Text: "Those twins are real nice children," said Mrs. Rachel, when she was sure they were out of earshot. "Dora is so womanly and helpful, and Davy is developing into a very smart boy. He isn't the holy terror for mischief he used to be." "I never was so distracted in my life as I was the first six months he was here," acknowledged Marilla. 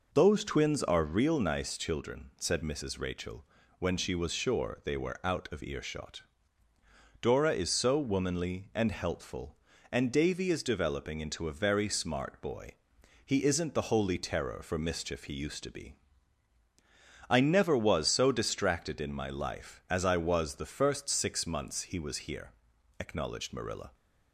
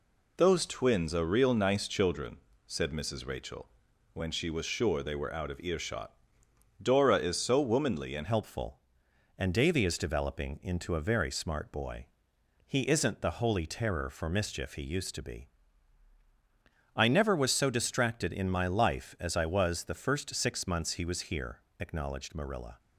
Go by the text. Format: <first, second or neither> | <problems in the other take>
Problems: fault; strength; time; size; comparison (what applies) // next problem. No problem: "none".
first | changes voice at "helpful"; from 8.2 s on; 14.5 s long